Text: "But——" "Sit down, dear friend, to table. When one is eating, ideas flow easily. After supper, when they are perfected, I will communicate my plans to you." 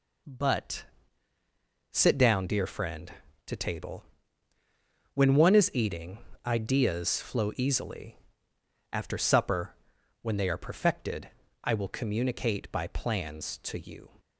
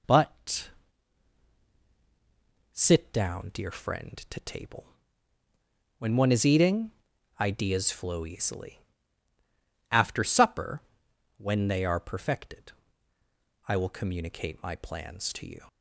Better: second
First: says "by" for "my"; at 12.7 s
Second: none

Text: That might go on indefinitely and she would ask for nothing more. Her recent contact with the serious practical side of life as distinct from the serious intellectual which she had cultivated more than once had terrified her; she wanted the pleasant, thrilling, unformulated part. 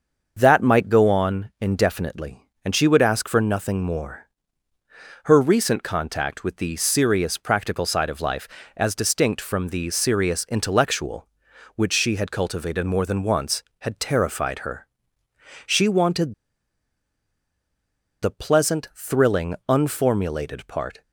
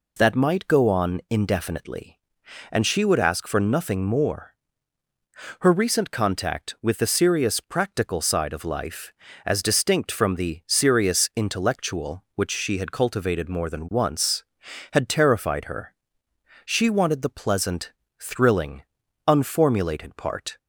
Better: second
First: starts louder than the rest; until 1.3 s; 6.5 dB // pauses between "wanted" and "the"; strong; at 16.3 s; 1.8 s long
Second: none

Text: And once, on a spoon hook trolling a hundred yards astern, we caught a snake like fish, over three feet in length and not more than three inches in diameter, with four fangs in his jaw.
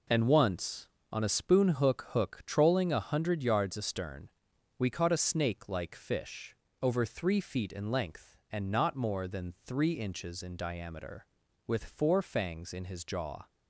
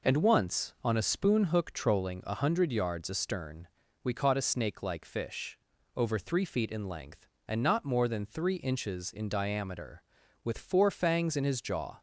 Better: second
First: says "hook" twice; at 2.1 s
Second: none

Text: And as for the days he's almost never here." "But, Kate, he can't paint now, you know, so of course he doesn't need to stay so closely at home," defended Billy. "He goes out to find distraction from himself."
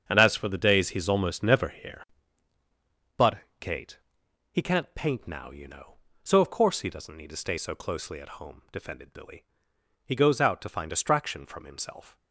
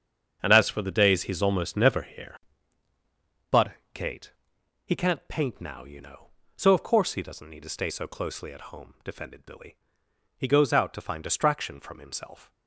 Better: neither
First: starts louder than the rest; strong; until 1.0 s; 7.5 dB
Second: starts louder than the rest; strong; until 1.4 s; 7.5 dB

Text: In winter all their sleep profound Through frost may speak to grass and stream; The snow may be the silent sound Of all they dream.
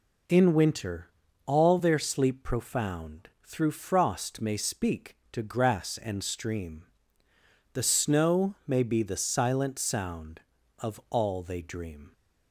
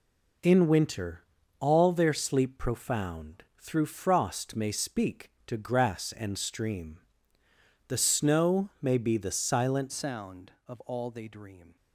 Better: first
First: pauses between "winter" and "all"; slight; at 1.1 s; 0.34 s long // pauses between "profound" and "Through"; slight; at 3.2 s; 0.16 s long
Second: pauses between "winter" and "all"; slight; at 1.2 s; 0.34 s long // pauses between "profound" and "Through"; slight; at 3.4 s; 0.16 s long // changes voice at "sound"; from 9.8 s on; 1.9 s long

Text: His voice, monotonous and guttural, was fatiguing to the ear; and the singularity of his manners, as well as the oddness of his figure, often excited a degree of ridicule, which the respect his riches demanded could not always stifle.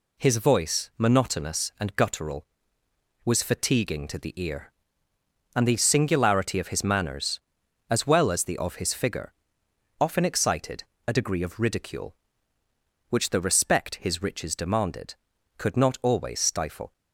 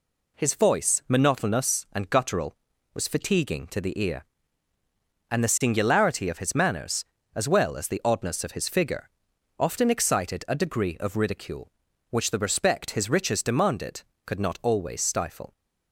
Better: second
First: skips "oddness"; at 8.5 s // pauses between "excited" and "a"; slight; at 10.8 s; 0.22 s long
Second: none

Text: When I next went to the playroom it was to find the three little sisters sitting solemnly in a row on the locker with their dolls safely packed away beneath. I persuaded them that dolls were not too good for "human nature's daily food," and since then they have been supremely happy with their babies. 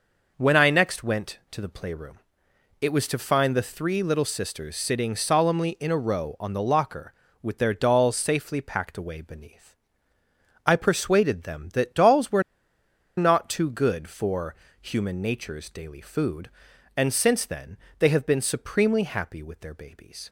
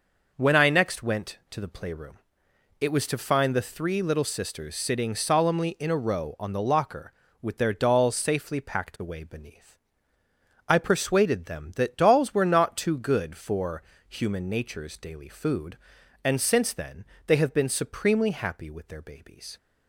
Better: second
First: pauses between "playroom" and "it"; noticeable; at 2.1 s; 0.62 s long // pauses between "were" and "not"; noticeable; at 12.4 s; 0.75 s long // pauses between "for" and "human"; slight; at 14.5 s; 0.26 s long // pauses between "then" and "they"; slight; at 17.7 s; 0.18 s long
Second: pauses between "playroom" and "it"; noticeable; at 2.1 s; 0.62 s long // pauses between "for" and "human"; slight; at 13.8 s; 0.26 s long // pauses between "then" and "they"; slight; at 17.0 s; 0.18 s long

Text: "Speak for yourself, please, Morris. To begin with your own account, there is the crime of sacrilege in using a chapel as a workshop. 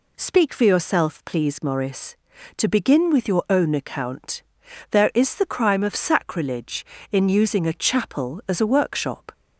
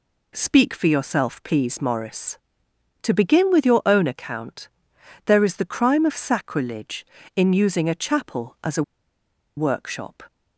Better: first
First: none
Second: pauses between "a" and "workshop"; noticeable; at 8.8 s; 0.74 s long

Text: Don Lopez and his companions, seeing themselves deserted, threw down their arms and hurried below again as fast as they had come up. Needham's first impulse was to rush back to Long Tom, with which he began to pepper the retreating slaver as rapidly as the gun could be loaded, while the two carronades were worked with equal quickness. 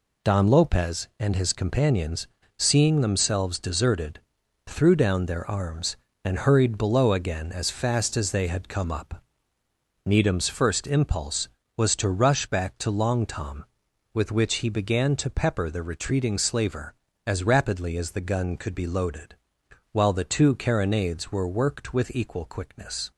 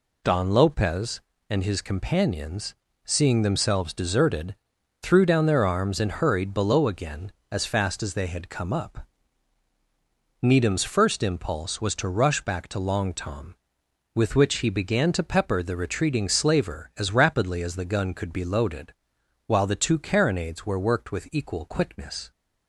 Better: neither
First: none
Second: none

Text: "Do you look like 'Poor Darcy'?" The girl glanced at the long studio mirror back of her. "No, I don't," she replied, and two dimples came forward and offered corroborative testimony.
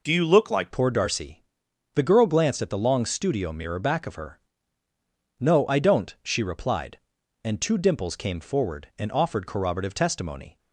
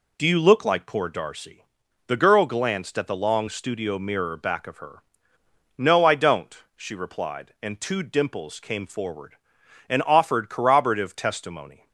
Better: second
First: changes voice at "Poor"; from 0.7 s on; 9.8 s long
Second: none

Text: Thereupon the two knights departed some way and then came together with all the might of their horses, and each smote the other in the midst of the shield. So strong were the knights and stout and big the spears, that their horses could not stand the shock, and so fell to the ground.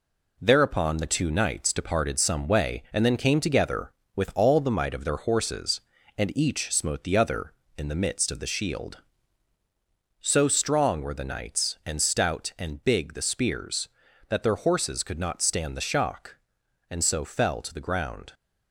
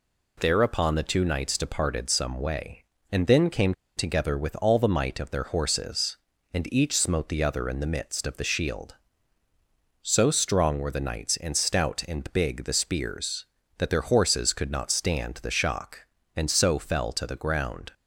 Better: first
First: none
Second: pauses between "came" and "together"; slight; at 3.7 s; 0.24 s long

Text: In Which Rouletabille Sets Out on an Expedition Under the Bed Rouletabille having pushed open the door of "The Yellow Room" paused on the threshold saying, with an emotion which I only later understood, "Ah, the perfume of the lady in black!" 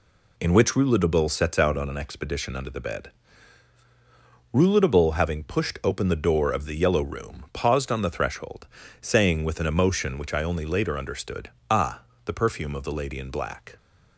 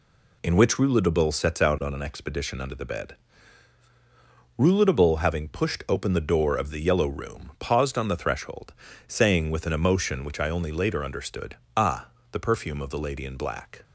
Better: neither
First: pauses between "Bed" and "Rouletabille"; strong; at 3.1 s; 1.4 s long // pauses between "threshold" and "saying"; slight; at 8.6 s; 0.34 s long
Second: pauses between "Bed" and "Rouletabille"; strong; at 3.1 s; 1.4 s long // pauses between "threshold" and "saying"; slight; at 8.7 s; 0.34 s long

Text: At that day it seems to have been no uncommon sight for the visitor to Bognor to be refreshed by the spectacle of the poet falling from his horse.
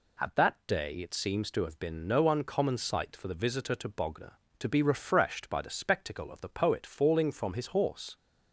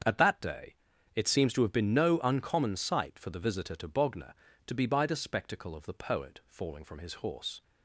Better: first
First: none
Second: starts louder than the rest; strong; until 1.4 s; 7.5 dB // pauses between "day" and "it"; at 0.7 s; 0.40 s long // skips "refreshed"; at 4.8 s

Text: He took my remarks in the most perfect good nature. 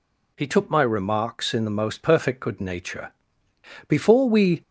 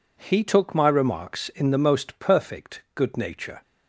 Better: second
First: goes on to say "Before we"; noticeable; from 3.8 s on; 0.74 s long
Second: none

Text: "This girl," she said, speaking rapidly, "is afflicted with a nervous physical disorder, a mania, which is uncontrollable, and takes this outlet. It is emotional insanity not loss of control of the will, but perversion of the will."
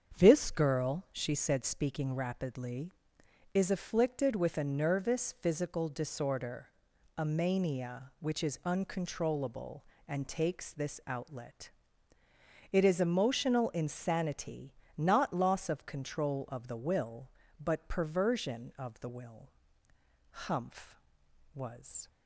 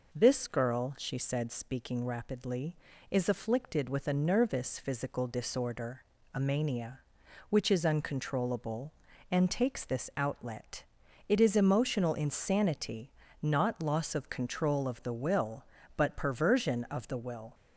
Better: second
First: starts louder than the rest; strong; until 1.2 s; 7 dB // pauses between "insanity" and "not"; slight; at 14.7 s; 0.24 s long // goes on to say "Humph was"; strong; from 20.3 s on; 1.7 s long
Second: pauses between "insanity" and "not"; slight; at 13.0 s; 0.32 s long

